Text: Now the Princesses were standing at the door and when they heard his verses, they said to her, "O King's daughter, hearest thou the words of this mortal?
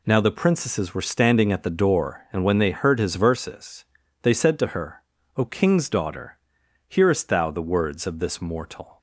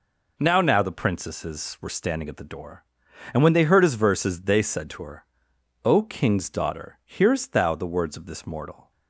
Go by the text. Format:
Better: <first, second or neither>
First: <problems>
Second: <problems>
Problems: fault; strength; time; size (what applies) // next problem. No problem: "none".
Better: first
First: none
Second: says "Now" twice; at 0.6 s